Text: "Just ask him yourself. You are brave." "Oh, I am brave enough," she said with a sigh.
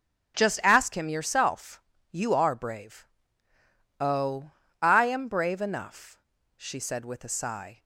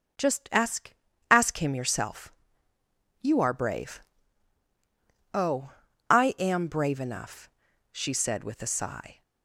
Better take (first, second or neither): first